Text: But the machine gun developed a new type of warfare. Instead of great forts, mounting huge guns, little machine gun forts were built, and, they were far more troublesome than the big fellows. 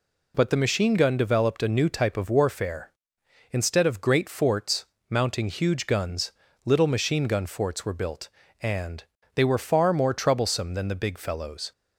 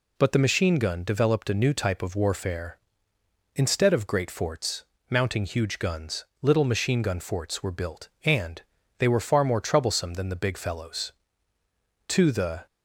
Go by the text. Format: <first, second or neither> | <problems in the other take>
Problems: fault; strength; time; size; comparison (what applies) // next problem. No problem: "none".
first | goes on to say "To the"; from 12.0 s on; 0.58 s long